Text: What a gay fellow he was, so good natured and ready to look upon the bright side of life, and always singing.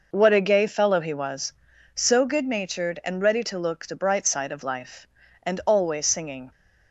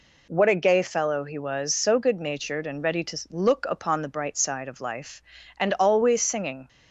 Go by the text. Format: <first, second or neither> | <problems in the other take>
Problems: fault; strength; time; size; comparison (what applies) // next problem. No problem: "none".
second | skips "upon"; at 3.8 s